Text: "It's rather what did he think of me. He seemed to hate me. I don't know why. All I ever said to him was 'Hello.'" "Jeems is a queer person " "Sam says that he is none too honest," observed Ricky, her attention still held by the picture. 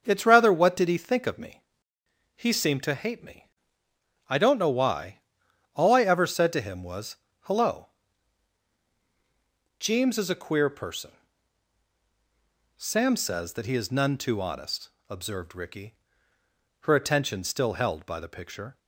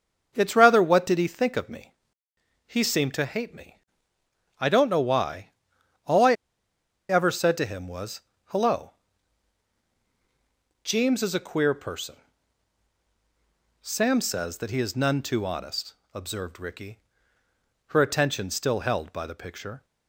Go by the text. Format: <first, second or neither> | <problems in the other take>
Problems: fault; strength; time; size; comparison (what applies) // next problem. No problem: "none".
first | starts louder than the rest; until 1.3 s; 6.5 dB; also in the first // pauses between "I" and "ever"; noticeable; at 6.3 s; 0.76 s long // pauses between "was" and "Hello"; slight; at 8.2 s; 0.22 s long; slight in the first